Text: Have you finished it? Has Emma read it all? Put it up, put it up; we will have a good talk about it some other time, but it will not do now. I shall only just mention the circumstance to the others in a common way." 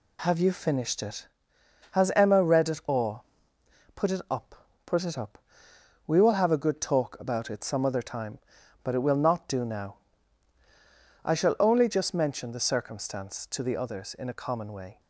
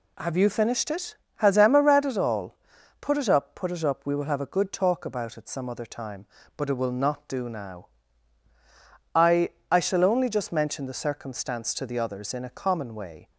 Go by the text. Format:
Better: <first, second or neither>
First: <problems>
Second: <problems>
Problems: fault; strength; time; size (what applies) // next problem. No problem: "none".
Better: first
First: none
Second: says "I" twice; at 9.7 s